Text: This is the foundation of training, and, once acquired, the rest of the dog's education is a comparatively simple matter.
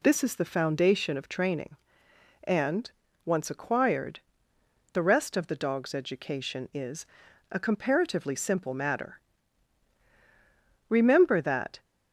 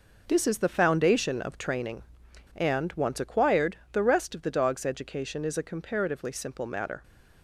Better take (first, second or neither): second